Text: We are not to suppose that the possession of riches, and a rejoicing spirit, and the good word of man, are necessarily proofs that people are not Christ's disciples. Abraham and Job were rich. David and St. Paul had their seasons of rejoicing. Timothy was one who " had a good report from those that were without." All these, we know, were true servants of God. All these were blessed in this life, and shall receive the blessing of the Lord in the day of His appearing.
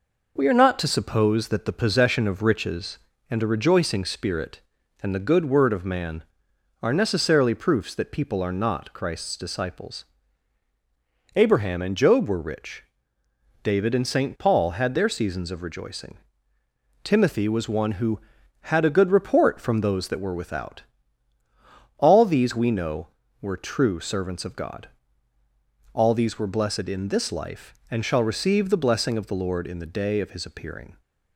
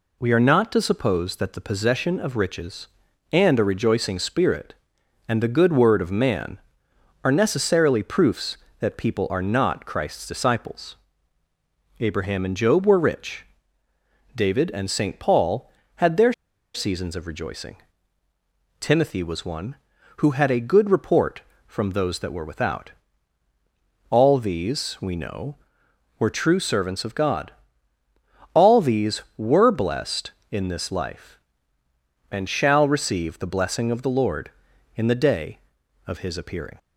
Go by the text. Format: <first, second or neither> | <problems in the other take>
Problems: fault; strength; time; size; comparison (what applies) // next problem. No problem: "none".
first | pauses between "their" and "seasons"; at 16.3 s; 0.42 s long